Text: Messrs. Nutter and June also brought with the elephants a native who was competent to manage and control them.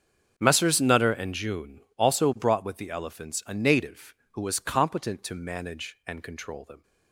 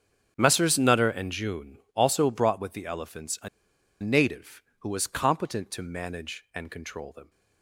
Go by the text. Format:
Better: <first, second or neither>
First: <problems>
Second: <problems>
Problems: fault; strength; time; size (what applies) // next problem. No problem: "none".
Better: first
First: starts louder than the rest; strong; until 1.3 s; 7 dB // pauses between "June" and "also"; slight; at 1.8 s; 0.16 s long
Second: starts louder than the rest; until 1.3 s; 7 dB // pauses between "June" and "also"; slight; at 1.7 s; 0.16 s long // pauses between "a" and "native"; noticeable; at 3.4 s; 0.53 s long